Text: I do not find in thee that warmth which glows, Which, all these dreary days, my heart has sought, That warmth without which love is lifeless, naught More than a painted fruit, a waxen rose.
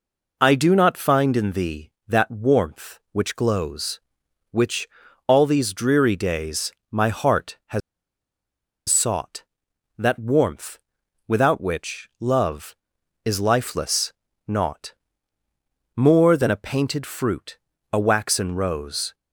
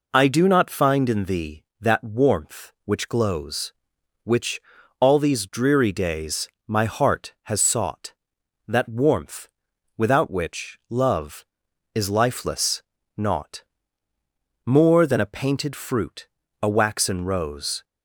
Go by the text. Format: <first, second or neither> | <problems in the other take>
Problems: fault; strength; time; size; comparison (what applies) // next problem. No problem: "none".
second | pauses between "has" and "sought"; at 7.8 s; 1.0 s long // pauses between "warmth" and "without"; noticeable; at 10.7 s; 0.50 s long; noticeable in the second // pauses between "naught" and "More"; at 14.9 s; 1.0 s long; also in the second